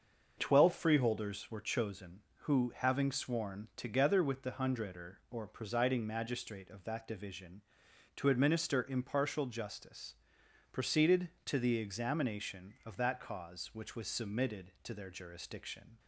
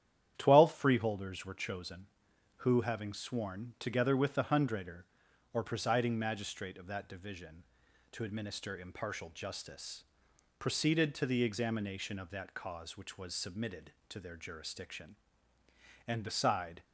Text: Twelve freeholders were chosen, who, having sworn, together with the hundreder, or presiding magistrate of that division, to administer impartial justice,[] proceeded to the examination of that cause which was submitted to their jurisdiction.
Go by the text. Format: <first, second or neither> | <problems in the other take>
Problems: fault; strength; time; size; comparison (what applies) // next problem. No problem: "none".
first | starts louder than the rest; strong; until 1.3 s; 10 dB; also in the first // goes on to say "And beside"; noticeable; from 16.0 s on; 0.76 s long